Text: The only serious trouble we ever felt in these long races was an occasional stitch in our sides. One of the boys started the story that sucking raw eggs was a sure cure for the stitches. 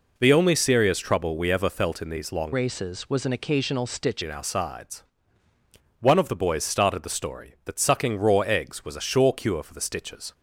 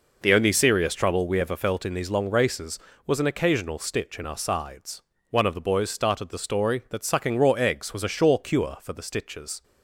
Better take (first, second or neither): second